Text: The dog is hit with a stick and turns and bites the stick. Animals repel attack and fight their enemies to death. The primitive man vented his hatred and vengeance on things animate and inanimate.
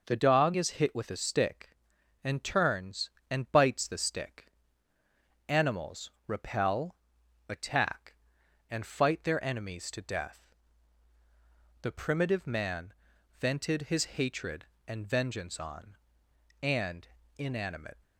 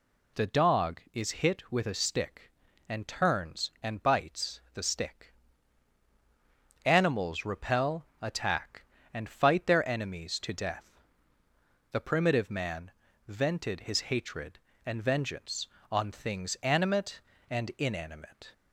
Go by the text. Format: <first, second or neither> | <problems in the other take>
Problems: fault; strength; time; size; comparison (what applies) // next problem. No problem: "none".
second | pauses between "Animals" and "repel"; slight; at 6.0 s; 0.16 s long // pauses between "repel" and "attack"; noticeable; at 6.9 s; 0.52 s long; slight in the second // pauses between "man" and "vented"; noticeable; at 12.9 s; 0.46 s long; slight in the second // skips "things animate"; at 16.2 s // pauses between "and" and "inanimate"; slight; at 17.0 s; 0.32 s long